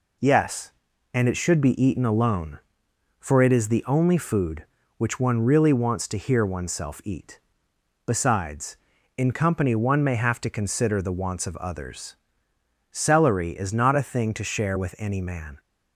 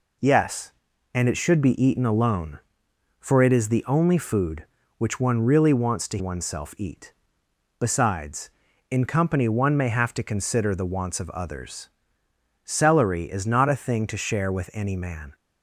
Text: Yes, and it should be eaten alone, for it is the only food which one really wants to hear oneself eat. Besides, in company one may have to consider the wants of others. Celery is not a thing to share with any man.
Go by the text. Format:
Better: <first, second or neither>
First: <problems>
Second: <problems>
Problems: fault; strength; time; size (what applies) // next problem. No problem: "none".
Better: first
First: none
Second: skips "hear"; at 6.1 s